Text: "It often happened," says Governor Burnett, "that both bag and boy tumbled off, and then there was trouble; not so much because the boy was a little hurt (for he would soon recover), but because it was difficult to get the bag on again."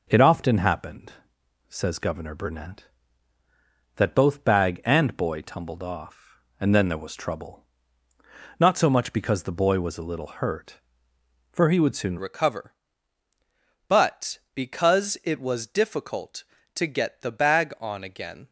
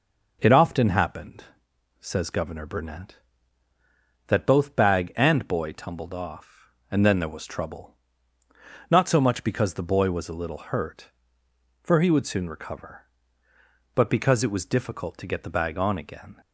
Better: second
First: changes voice at "recover"; from 12.1 s on; 6.3 s long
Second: none

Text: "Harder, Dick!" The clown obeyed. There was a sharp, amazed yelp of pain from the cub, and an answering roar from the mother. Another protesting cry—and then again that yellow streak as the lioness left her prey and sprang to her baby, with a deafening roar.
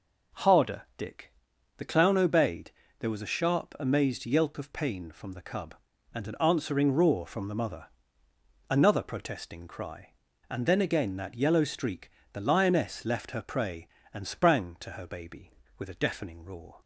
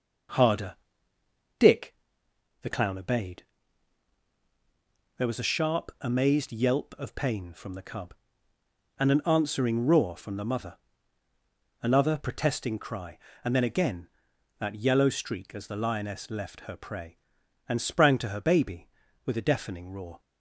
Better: second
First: skips "as"; at 12.2 s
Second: none

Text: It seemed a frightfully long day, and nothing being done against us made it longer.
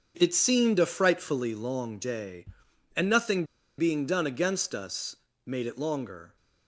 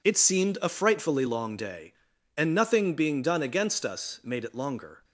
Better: second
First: starts louder than the rest; until 1.1 s; 7 dB // pauses between "nothing" and "being"; slight; at 3.4 s; 0.34 s long // pauses between "us" and "made"; slight; at 5.1 s; 0.30 s long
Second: none

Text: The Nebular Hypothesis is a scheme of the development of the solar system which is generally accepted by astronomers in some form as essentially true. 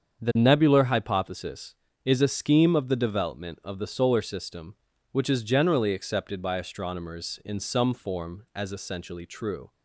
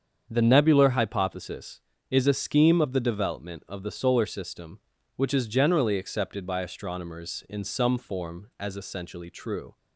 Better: neither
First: starts louder than the rest; strong; until 1.2 s; 7 dB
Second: starts louder than the rest; strong; until 1.3 s; 7 dB

